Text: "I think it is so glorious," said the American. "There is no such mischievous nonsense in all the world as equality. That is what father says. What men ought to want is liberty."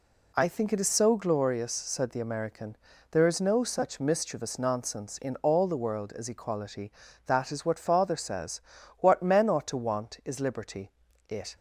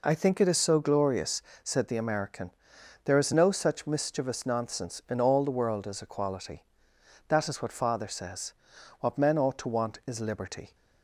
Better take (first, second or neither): second